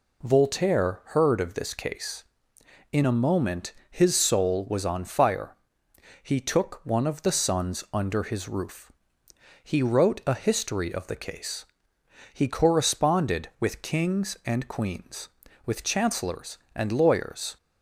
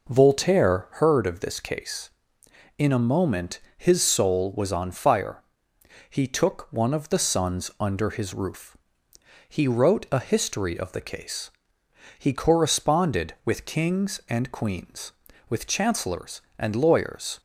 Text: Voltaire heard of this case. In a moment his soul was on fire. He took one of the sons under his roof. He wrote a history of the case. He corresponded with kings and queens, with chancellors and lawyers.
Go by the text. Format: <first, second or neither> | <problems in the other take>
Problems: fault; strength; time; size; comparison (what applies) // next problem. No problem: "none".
first | starts louder than the rest; noticeable; until 1.1 s; 5 dB // pauses between "moment" and "his"; slight; at 3.5 s; 0.16 s long; slight in the first